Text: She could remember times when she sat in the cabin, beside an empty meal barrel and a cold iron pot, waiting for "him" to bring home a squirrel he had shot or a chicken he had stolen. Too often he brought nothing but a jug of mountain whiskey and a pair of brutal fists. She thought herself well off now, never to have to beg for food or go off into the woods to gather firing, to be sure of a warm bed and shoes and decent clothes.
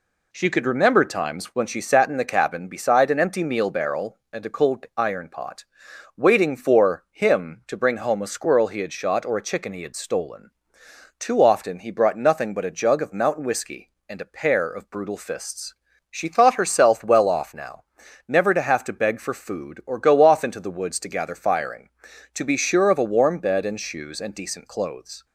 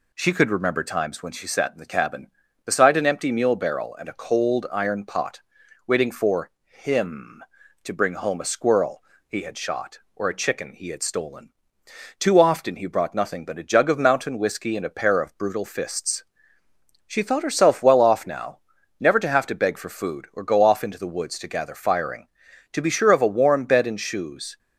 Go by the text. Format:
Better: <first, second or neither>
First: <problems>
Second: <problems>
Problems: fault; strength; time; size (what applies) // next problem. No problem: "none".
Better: first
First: none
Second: pauses between "for" and "him"; slight; at 6.5 s; 0.16 s long // pauses between "squirrel" and "he"; slight; at 9.0 s; 0.24 s long // stops before "and decent clothes"; at 24.5 s